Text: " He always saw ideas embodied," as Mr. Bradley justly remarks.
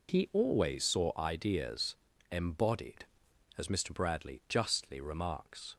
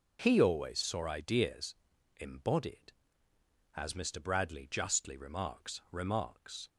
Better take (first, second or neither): first